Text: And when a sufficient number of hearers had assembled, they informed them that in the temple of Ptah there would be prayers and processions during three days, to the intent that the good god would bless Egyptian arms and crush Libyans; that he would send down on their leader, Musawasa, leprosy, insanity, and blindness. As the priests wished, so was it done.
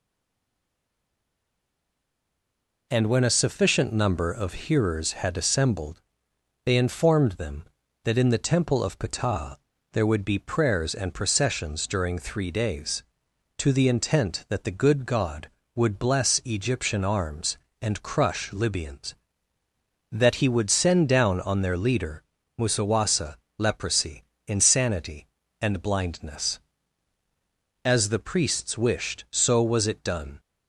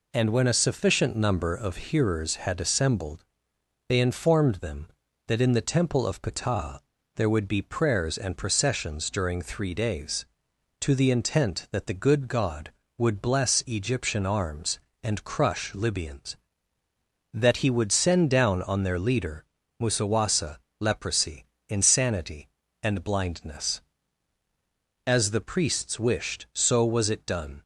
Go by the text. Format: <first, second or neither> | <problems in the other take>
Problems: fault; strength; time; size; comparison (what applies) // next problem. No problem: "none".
second | stays silent before the first word; strong; until 2.9 s; 2.9 s long // pauses between "Ptah" and "there"; slight; at 9.5 s; 0.36 s long; slight in the second